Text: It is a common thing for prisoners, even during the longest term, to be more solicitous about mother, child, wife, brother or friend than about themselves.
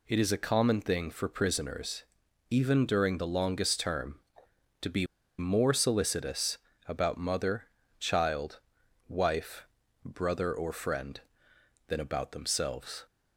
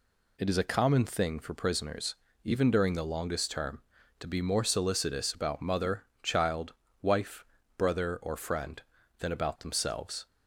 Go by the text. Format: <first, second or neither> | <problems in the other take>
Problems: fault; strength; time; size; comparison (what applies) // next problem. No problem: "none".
second | pauses between "be" and "more"; slight; at 5.0 s; 0.32 s long // pauses between "solicitous" and "about"; slight; at 6.5 s; 0.30 s long